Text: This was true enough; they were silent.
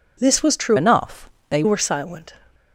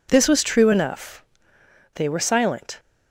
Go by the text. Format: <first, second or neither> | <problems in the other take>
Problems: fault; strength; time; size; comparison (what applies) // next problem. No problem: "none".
second | changes voice from "enough" to "they"; from 0.7 to 1.6 s; 0.9 s long